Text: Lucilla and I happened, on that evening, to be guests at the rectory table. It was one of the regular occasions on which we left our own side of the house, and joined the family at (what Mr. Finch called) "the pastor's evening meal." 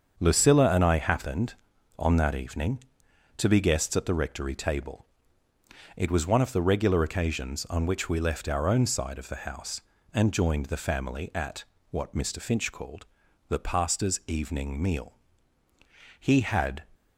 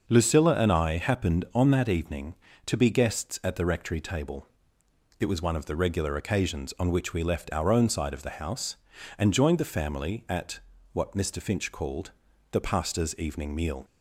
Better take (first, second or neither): second